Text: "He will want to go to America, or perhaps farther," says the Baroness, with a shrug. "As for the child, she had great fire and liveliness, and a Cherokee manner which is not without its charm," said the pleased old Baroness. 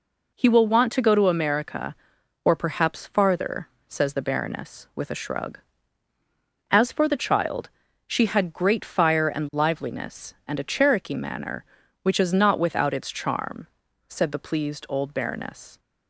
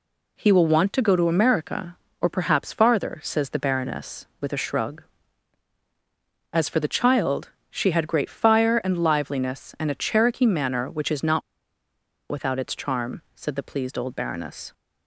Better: first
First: none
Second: pauses between "not" and "without"; noticeable; at 11.4 s; 0.89 s long

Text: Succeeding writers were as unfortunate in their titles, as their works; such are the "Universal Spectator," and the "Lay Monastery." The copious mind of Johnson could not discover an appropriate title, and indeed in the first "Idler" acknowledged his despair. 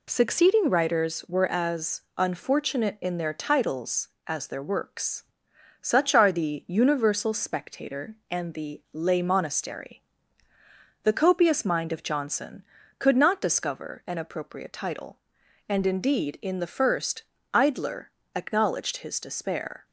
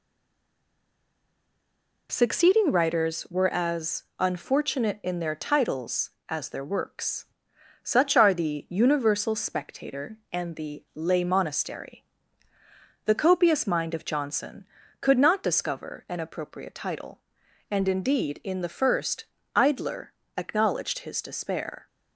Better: first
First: pauses between "as" and "unfortunate"; slight; at 2.0 s; 0.16 s long // pauses between "first" and "Idler"; slight; at 17.2 s; 0.32 s long // pauses between "Idler" and "acknowledged"; slight; at 18.0 s; 0.26 s long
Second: stays silent before the first word; noticeable; until 2.0 s; 2.0 s long // pauses between "as" and "unfortunate"; slight; at 4.0 s; 0.16 s long // pauses between "first" and "Idler"; slight; at 19.2 s; 0.32 s long // pauses between "Idler" and "acknowledged"; slight; at 20.1 s; 0.26 s long

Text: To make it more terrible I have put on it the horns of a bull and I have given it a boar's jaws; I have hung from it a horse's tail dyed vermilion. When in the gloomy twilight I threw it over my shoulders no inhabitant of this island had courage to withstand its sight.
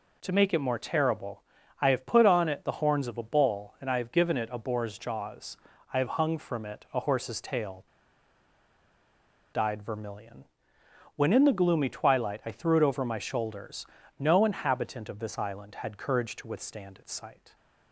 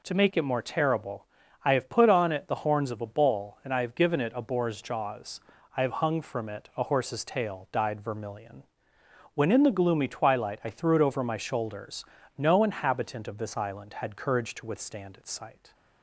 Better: second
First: pauses between "terrible" and "I"; at 1.4 s; 0.38 s long // pauses between "tail" and "dyed"; strong; at 7.8 s; 1.6 s long // pauses between "shoulders" and "no"; slight; at 13.8 s; 0.32 s long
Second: pauses between "terrible" and "I"; at 1.2 s; 0.38 s long // pauses between "shoulders" and "no"; slight; at 12.0 s; 0.32 s long

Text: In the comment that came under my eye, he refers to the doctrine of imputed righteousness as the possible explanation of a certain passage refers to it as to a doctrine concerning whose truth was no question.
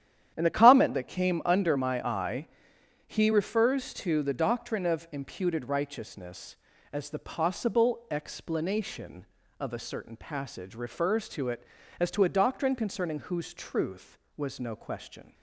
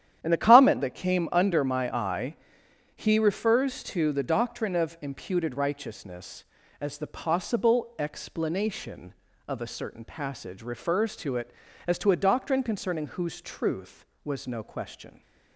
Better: neither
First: starts louder than the rest; strong; until 1.3 s; 10 dB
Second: starts louder than the rest; strong; until 1.2 s; 10 dB

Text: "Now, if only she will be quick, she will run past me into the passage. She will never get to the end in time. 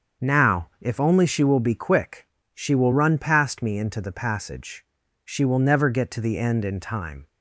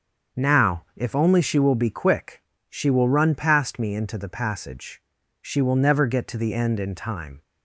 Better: neither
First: starts louder than the rest; until 1.3 s; 7 dB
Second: starts louder than the rest; until 1.4 s; 7 dB

